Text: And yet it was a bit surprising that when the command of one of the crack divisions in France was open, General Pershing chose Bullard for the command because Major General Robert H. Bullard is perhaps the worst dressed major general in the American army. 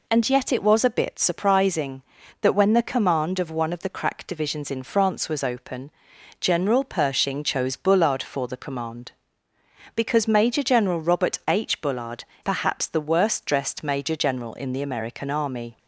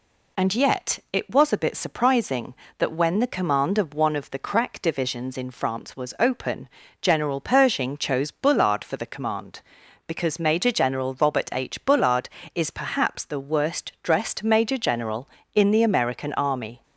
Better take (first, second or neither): second